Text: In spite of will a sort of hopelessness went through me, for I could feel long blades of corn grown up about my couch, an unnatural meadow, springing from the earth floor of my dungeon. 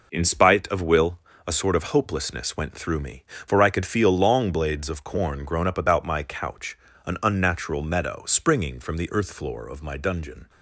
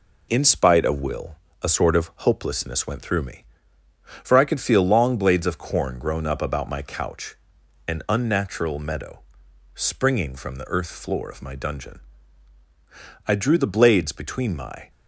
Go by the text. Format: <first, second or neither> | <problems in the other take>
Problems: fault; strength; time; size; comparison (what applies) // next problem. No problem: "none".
first | pauses between "will" and "a"; slight; at 1.3 s; 0.26 s long; slight in the first // goes on to say "I drew the blades between my"; from 13.2 s on; 1.6 s long